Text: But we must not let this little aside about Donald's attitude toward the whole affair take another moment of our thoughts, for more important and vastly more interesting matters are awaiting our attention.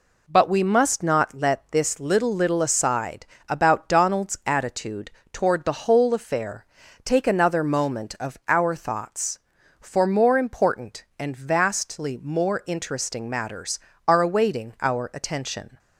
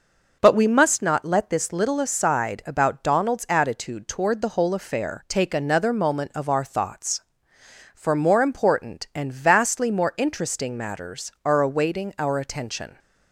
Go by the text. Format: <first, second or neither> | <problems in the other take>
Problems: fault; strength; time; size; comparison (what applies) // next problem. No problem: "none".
second | says "little" twice; at 2.3 s // pauses between "aside" and "about"; slight; at 3.2 s; 0.22 s long // pauses between "attitude" and "toward"; slight; at 5.1 s; 0.22 s long // pauses between "affair" and "take"; at 6.6 s; 0.40 s long